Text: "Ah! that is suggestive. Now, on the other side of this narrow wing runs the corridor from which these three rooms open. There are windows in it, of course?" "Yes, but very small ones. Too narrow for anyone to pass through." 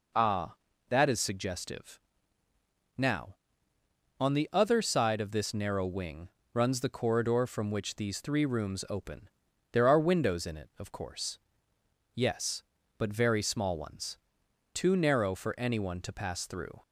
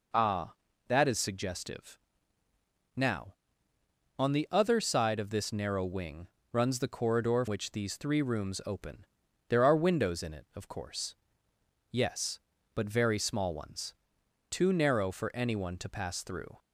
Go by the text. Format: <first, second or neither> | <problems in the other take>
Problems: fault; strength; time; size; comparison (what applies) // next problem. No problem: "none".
first | pauses between "wing" and "runs"; slight; at 6.2 s; 0.24 s long; slight in the first // skips "from"; at 7.4 s